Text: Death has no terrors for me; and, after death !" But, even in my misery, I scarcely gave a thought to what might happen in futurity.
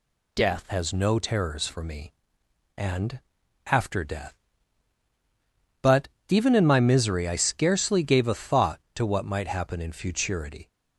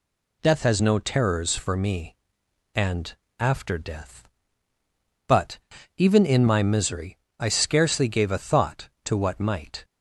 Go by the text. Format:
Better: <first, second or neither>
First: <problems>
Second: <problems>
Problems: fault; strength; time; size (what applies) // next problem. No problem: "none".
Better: first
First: none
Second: stops before "happen in futurity"; at 9.8 s